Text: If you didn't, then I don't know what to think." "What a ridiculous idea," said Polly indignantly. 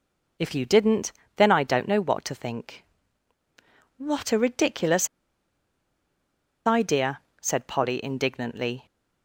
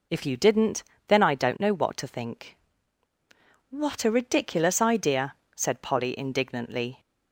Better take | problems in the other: second | pauses between "ridiculous" and "idea"; strong; at 5.0 s; 1.5 s long

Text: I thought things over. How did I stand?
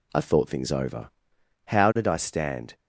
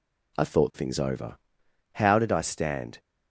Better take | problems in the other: neither | none

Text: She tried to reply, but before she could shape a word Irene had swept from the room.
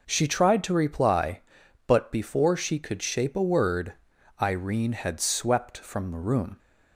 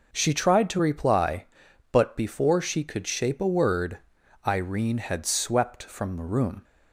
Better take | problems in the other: neither | pauses between "word" and "Irene"; the same in both

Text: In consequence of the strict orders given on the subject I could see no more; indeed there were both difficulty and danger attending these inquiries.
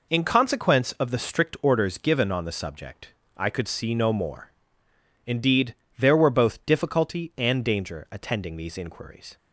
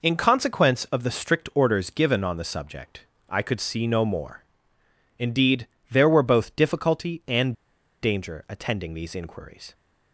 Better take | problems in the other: first | pauses between "subject" and "I"; slight; at 3.0 s; 0.24 s long; slight in the first // pauses between "indeed" and "there"; slight; at 5.6 s; 0.24 s long; slight in the first // pauses between "and" and "danger"; noticeable; at 7.5 s; 0.49 s long

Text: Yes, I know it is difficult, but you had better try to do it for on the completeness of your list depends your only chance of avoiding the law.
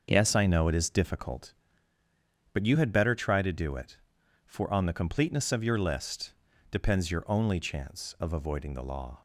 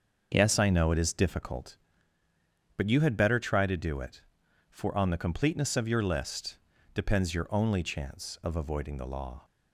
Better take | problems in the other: neither | starts louder than the rest; the same in both // pauses between "list" and "depends"; the same in both

